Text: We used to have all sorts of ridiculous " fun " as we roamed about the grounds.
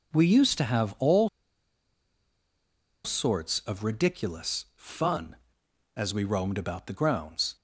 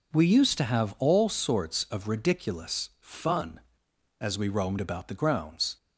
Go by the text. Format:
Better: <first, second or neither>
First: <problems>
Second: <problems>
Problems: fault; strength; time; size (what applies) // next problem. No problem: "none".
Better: second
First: pauses between "all" and "sorts"; strong; at 1.2 s; 1.7 s long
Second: none